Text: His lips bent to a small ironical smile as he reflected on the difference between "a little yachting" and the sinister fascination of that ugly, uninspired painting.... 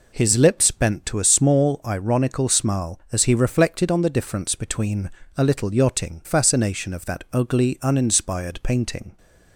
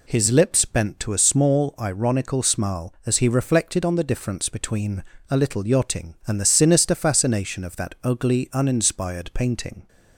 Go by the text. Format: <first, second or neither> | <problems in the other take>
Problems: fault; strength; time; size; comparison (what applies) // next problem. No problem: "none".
second | pauses between "between" and "a"; slight; at 5.0 s; 0.30 s long; slight in the second // skips "and the sinister"; at 6.2 s